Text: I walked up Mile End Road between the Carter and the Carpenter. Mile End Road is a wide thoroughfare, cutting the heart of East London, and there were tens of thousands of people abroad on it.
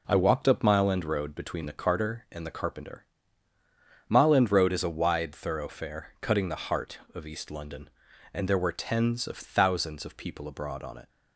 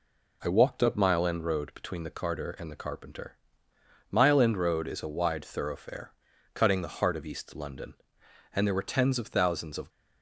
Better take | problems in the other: first | stops before "people abroad on it"; at 9.8 s

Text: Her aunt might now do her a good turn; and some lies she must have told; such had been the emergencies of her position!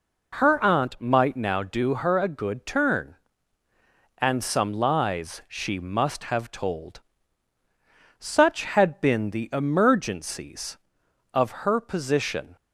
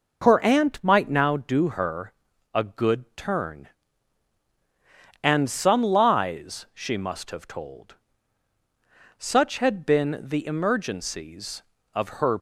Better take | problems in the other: first | pauses between "her" and "a"; at 2.1 s; 0.42 s long // stops before "position"; at 12.3 s

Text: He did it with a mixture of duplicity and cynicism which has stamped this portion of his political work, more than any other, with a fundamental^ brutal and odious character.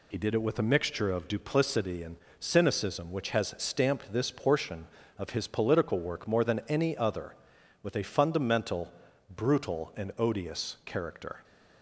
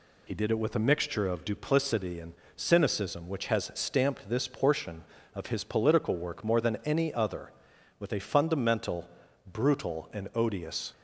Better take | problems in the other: first | pauses between "and" and "cynicism"; slight; at 2.3 s; 0.20 s long; slight in the first // pauses between "fundamental" and "brutal"; at 9.0 s; 0.42 s long; also in the first // stops before "character"; at 10.9 s

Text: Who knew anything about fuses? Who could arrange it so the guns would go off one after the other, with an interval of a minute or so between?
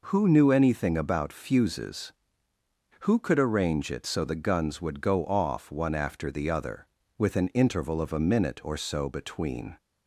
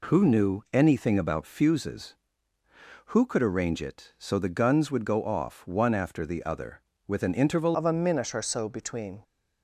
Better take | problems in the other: first | changes voice at "of"; from 7.7 s on; 1.5 s long

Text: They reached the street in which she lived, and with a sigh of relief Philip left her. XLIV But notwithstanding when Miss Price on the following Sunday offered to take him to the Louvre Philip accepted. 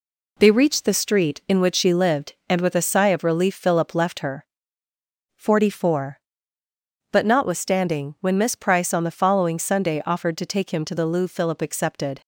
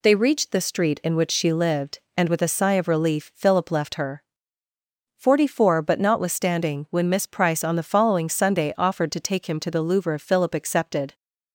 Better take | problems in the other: neither | none

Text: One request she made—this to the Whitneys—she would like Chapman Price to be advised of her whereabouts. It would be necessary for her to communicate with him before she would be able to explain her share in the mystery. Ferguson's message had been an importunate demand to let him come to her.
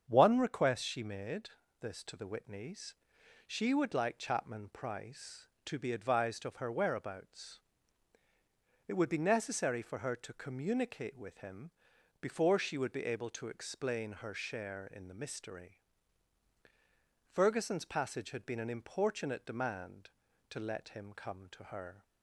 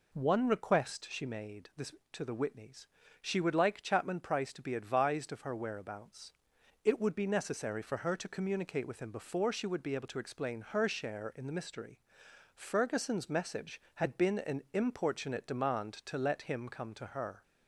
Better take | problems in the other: second | starts louder than the rest; strong; until 1.0 s; 7.5 dB // pauses between "him" and "before"; noticeable; at 11.7 s; 0.50 s long // says "passage" for "message"; at 17.8 s

